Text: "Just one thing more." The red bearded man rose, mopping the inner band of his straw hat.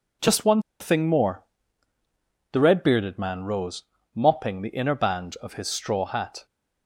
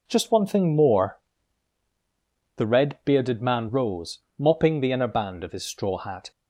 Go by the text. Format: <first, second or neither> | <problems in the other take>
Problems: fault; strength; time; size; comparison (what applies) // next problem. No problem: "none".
second | pauses between "one" and "thing"; slight; at 0.6 s; 0.18 s long